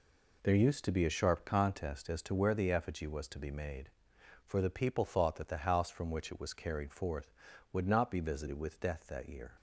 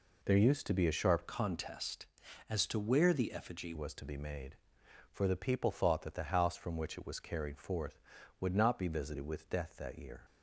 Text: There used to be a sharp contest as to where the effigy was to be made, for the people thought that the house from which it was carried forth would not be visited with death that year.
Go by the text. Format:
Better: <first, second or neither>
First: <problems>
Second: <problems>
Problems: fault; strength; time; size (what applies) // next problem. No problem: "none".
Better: first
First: none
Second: changes voice from "contest" to "effigy"; from 1.2 to 3.7 s; 2.5 s long